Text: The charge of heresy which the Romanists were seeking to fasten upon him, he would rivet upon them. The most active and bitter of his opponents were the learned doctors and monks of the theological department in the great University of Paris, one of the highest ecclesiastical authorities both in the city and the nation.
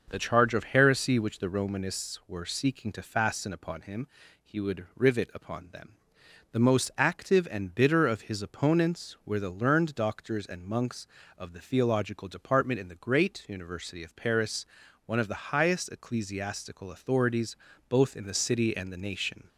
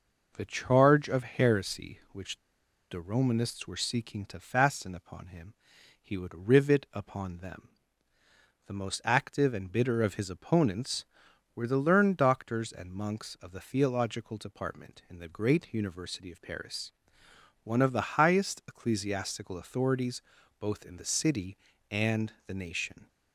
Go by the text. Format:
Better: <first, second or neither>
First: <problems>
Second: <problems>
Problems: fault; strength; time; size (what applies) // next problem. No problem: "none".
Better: first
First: pauses between "authorities" and "both"; slight; at 17.5 s; 0.30 s long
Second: pauses between "which" and "the"; noticeable; at 2.3 s; 0.54 s long // pauses between "authorities" and "both"; at 20.2 s; 0.38 s long